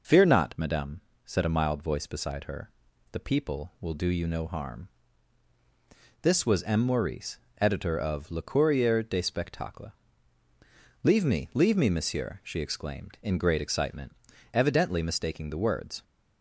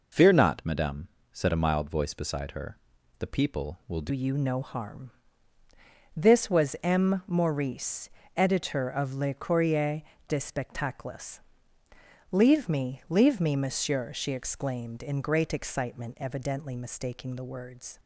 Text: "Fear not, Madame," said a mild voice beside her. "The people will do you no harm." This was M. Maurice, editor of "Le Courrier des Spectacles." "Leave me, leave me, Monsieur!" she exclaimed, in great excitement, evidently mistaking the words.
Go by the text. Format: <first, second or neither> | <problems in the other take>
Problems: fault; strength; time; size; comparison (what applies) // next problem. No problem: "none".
first | changes voice at "you"; from 4.0 s on; 13.9 s long // pauses between "Courrier" and "des"; slight; at 10.0 s; 0.26 s long